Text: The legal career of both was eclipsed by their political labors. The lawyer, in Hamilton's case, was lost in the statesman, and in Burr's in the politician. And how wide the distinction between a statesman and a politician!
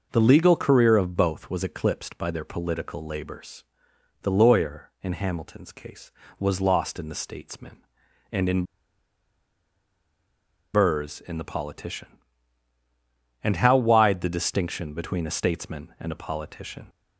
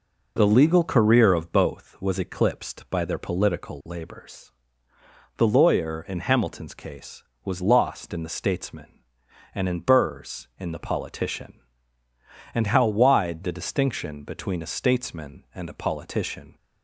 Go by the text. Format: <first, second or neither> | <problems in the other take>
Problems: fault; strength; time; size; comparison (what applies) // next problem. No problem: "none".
second | pauses between "in" and "Burr's"; strong; at 8.6 s; 2.1 s long